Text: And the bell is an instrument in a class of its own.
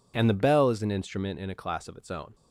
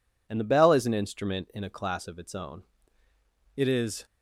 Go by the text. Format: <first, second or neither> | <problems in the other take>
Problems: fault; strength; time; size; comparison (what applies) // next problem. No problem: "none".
first | goes on to say "It is"; slight; from 3.5 s on; 0.48 s long